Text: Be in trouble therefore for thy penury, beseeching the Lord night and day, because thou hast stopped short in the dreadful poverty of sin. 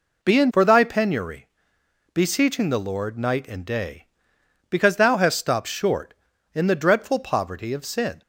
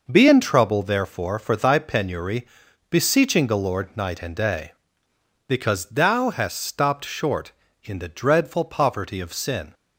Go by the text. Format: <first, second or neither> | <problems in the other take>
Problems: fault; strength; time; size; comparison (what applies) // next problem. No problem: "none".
second | skips "trouble therefore"; at 0.5 s